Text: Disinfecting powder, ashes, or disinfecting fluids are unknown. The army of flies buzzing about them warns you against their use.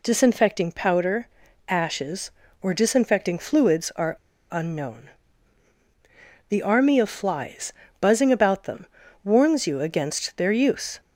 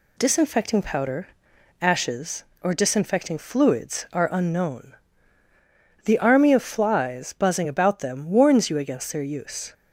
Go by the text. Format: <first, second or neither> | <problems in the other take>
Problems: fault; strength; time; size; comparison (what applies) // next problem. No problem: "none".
second | pauses between "are" and "unknown"; slight; at 4.1 s; 0.36 s long // pauses between "flies" and "buzzing"; slight; at 7.7 s; 0.28 s long // pauses between "them" and "warns"; at 8.8 s; 0.38 s long